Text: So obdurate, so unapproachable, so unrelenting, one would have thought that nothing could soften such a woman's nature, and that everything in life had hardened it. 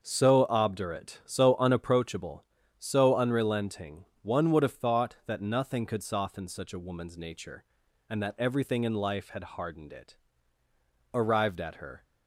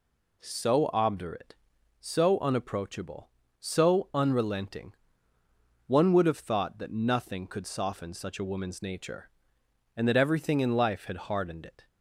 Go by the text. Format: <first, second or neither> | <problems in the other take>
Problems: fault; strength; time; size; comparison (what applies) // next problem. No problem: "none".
second | starts louder than the rest; until 1.0 s; 6.5 dB // goes on to say "Arrived at her"; noticeable; from 11.1 s on; 0.90 s long